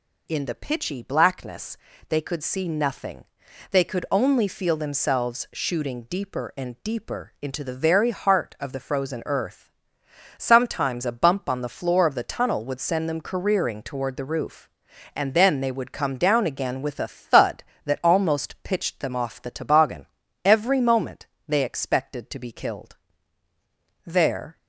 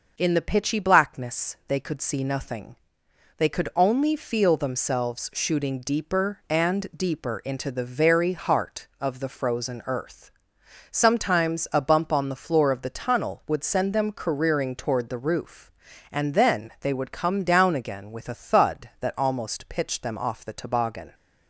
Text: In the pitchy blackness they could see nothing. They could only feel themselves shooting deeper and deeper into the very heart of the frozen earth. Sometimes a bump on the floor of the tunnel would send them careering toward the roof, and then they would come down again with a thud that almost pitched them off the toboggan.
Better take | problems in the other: second | pauses between "blackness" and "they"; slight; at 1.7 s; 0.30 s long // goes on to say "Every moment they expected to be killed There"; strong; from 20.4 s on; 4.1 s long

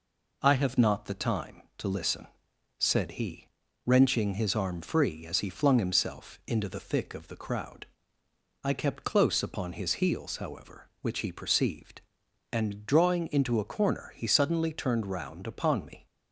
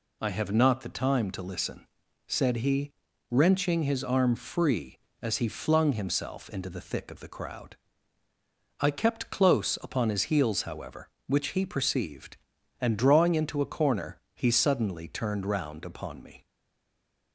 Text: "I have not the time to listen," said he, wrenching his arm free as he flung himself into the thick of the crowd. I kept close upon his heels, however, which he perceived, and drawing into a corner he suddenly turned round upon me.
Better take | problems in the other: first | pauses between "corner" and "he"; slight; at 14.1 s; 0.16 s long // stays silent after the last word; slight; from 16.4 s on; 0.9 s long

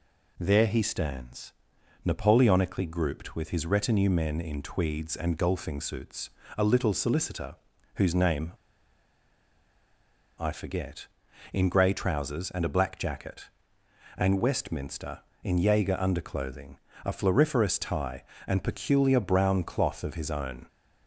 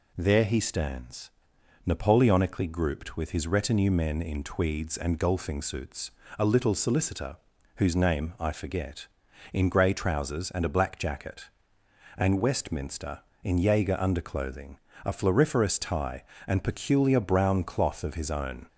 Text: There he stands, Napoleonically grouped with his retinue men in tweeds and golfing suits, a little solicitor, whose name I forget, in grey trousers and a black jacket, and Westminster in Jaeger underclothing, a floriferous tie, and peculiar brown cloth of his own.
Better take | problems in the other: second | pauses between "name" and "I"; strong; at 8.5 s; 1.8 s long

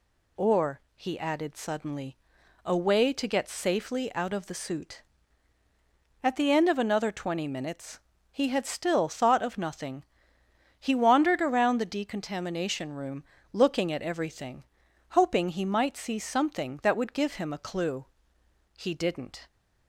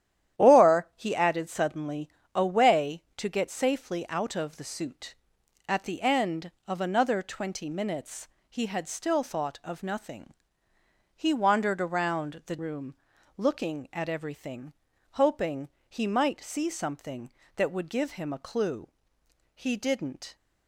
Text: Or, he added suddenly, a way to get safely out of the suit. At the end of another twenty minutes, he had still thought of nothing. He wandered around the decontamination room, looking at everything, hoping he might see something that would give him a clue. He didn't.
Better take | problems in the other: first | starts louder than the rest; strong; until 1.4 s; 11 dB // skips "decontamination"; at 12.5 s // pauses between "hoping" and "he"; slight; at 15.6 s; 0.18 s long

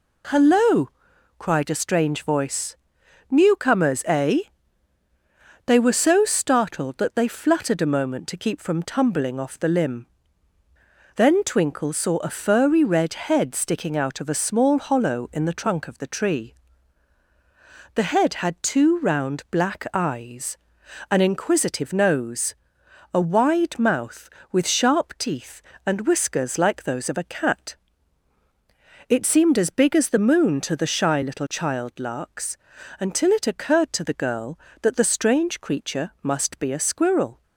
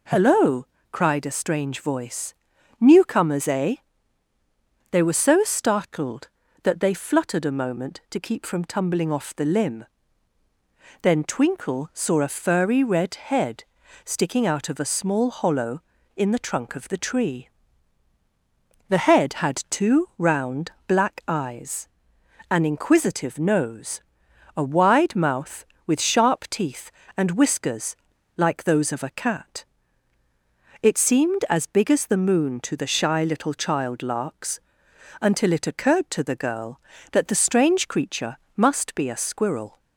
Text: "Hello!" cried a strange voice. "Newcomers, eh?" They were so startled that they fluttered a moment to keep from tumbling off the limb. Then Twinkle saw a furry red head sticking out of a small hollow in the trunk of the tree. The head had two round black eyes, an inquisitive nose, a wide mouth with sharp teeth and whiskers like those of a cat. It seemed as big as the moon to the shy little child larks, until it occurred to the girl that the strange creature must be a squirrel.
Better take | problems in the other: first | pauses between "head" and "sticking"; at 13.6 s; 0.40 s long // pauses between "round" and "black"; slight; at 20.7 s; 0.16 s long // pauses between "whiskers" and "like"; at 27.9 s; 0.38 s long // pauses between "creature" and "must"; slight; at 38.3 s; 0.18 s long

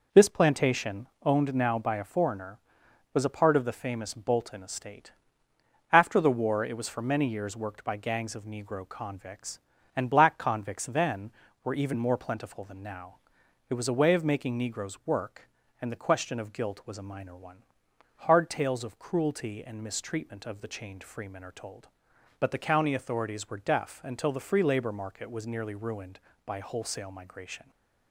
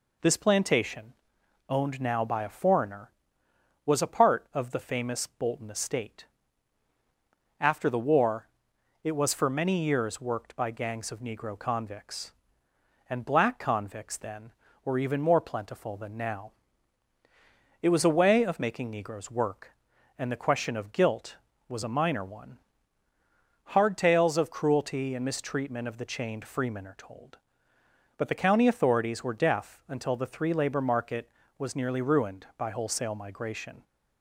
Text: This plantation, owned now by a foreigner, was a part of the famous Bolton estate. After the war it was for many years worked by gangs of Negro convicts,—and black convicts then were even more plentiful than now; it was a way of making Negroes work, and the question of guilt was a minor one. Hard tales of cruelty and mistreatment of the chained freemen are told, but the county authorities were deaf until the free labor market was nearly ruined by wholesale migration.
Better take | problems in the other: first | pauses between "war" and "it"; noticeable; at 8.4 s; 0.54 s long // says "three" for "free"; at 30.2 s

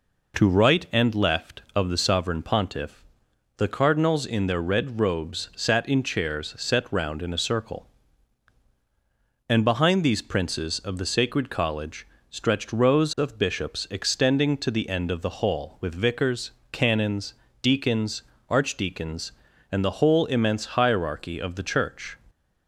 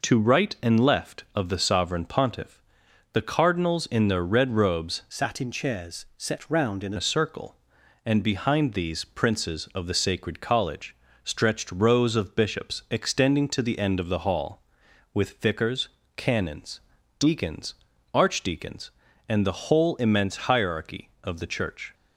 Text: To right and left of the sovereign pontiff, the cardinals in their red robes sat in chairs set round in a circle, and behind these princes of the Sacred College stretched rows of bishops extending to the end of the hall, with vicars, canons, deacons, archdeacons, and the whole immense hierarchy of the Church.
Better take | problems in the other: first | changes voice from "sat" to "in"; from 5.0 to 6.9 s; 1.9 s long // pauses between "College" and "stretched"; slight; at 10.9 s; 0.30 s long; slight in the first

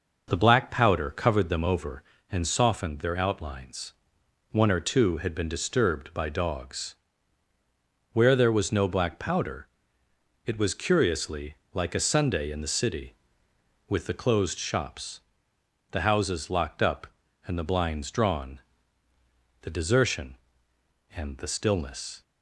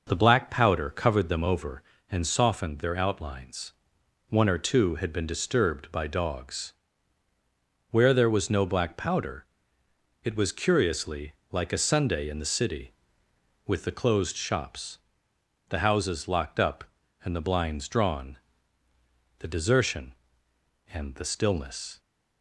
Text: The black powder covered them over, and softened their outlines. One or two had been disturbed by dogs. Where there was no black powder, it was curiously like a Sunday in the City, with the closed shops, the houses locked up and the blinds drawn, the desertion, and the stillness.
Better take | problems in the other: neither | pauses between "curiously" and "like"; slight; the same in both

